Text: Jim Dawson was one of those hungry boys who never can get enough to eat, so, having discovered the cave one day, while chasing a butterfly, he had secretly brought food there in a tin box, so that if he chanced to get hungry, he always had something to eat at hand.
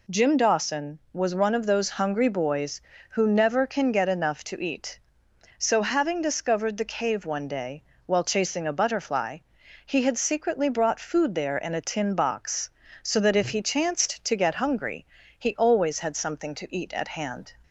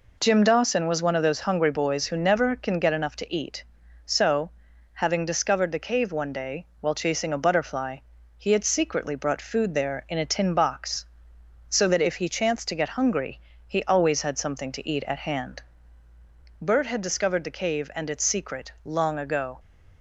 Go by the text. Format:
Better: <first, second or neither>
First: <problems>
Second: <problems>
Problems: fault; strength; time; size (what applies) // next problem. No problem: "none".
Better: first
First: none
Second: goes on to say "Bert had discovered the cave and its secret long ago"; strong; from 16.5 s on; 3.0 s long